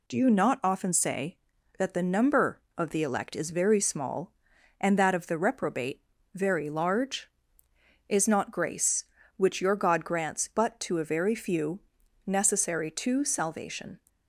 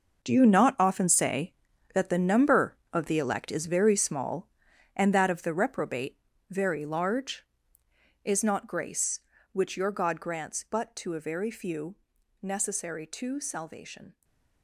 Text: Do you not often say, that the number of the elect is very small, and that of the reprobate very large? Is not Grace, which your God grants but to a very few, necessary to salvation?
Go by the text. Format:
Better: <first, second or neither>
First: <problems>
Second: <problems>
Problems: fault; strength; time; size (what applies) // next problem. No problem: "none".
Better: first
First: pauses between "reprobate" and "very"; slight; at 6.0 s; 0.32 s long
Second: gets quieter; strong; throughout; 11.5 dB // pauses between "reprobate" and "very"; slight; at 6.1 s; 0.32 s long // stays silent after the last word; slight; from 14.1 s on; 0.5 s long